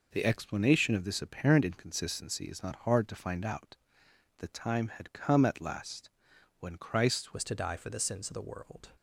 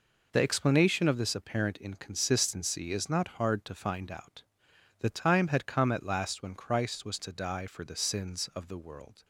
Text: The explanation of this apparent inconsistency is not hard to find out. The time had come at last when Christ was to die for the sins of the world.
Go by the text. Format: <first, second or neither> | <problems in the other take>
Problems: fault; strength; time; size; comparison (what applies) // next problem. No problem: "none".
second | pauses between "last" and "when"; noticeable; at 6.0 s; 0.50 s long // changes voice at "was"; from 7.3 s on; 1.5 s long